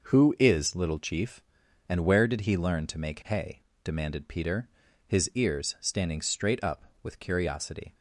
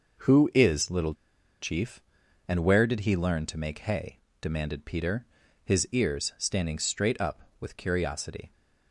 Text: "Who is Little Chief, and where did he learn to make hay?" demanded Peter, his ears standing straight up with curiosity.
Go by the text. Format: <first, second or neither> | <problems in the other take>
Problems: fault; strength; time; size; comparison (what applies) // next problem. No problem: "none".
first | pauses between "Little" and "Chief"; noticeable; at 1.1 s; 0.46 s long